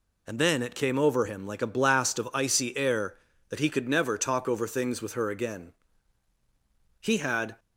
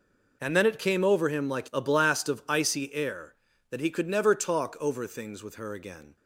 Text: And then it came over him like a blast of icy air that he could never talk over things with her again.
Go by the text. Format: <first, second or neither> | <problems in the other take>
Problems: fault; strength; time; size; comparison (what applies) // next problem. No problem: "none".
second | goes on to say "He had"; from 6.9 s on; 0.60 s long